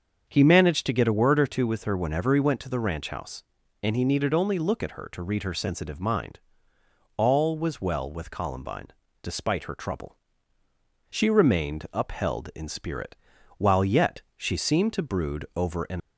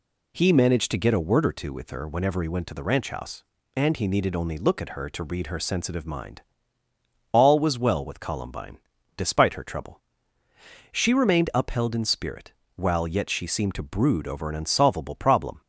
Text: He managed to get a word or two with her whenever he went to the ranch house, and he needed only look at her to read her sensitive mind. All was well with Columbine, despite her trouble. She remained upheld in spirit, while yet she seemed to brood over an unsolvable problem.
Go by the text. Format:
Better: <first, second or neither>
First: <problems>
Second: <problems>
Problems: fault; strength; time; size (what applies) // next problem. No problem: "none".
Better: second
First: starts louder than the rest; until 1.3 s; 7 dB // pauses between "yet" and "she"; slight; at 14.2 s; 0.16 s long // stops before "unsolvable problem"; at 16.0 s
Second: none